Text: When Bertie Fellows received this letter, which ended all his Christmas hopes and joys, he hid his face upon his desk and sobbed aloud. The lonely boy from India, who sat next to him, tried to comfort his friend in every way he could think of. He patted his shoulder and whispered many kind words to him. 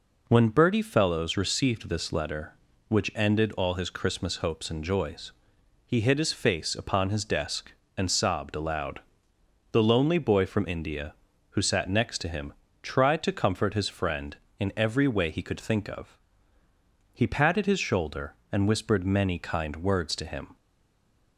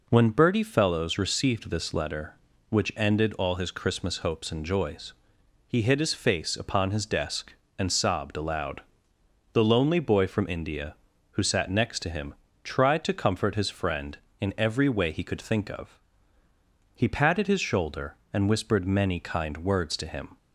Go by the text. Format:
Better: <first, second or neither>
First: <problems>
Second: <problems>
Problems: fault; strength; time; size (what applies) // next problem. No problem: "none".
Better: second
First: stays silent after the last word; slight; from 20.5 s on; 0.8 s long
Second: none